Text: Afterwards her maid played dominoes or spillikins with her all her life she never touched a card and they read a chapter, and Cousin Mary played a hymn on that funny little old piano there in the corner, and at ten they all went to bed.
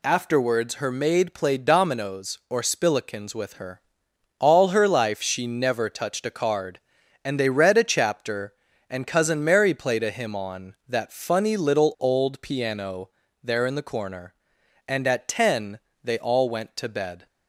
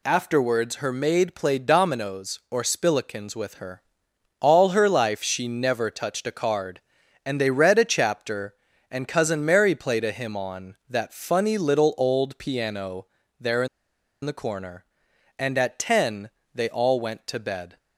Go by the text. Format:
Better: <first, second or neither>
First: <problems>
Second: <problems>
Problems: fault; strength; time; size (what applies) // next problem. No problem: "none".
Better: first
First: pauses between "her" and "all"; noticeable; at 3.7 s; 0.60 s long // pauses between "piano" and "there"; slight; at 13.0 s; 0.34 s long // pauses between "ten" and "they"; slight; at 15.8 s; 0.24 s long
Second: pauses between "her" and "all"; noticeable; at 3.8 s; 0.60 s long // pauses between "piano" and "there"; slight; at 13.0 s; 0.34 s long // pauses between "in" and "the"; noticeable; at 13.6 s; 0.56 s long // pauses between "ten" and "they"; slight; at 16.3 s; 0.24 s long